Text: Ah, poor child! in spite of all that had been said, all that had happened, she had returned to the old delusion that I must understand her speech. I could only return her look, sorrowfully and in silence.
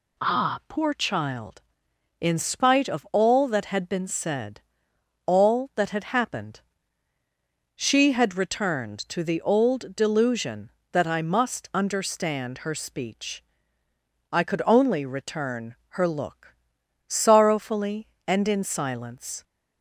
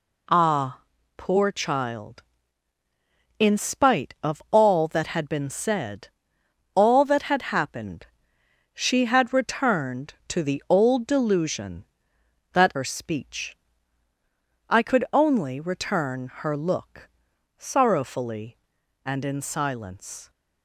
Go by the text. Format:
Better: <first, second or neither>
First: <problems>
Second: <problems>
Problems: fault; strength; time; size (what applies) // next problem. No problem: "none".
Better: first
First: none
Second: skips "I must understand"; at 12.7 s